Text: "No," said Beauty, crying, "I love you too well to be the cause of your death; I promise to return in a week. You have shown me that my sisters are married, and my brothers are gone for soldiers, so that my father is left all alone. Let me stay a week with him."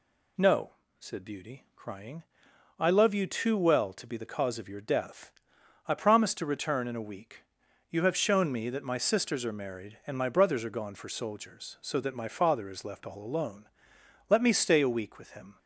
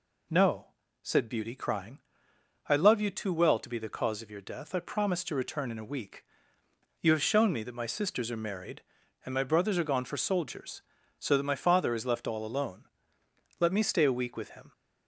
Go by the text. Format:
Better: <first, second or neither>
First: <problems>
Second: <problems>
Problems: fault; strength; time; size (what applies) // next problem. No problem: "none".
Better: neither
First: none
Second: none